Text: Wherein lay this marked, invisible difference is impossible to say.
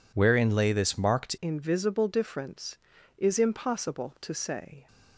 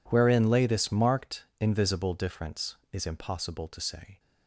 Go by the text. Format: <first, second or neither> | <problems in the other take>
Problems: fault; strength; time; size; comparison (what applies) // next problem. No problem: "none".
second | changes voice at "invisible"; from 1.3 s on; 3.5 s long